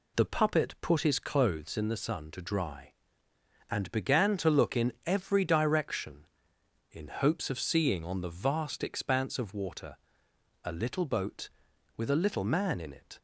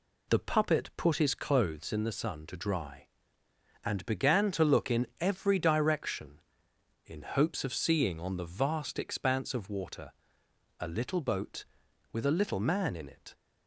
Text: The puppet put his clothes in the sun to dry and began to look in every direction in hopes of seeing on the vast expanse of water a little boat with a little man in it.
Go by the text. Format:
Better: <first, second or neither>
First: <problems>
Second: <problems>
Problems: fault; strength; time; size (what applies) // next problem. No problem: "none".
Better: neither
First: pauses between "water" and "a"; noticeable; at 9.9 s; 0.68 s long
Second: pauses between "water" and "a"; noticeable; at 10.1 s; 0.68 s long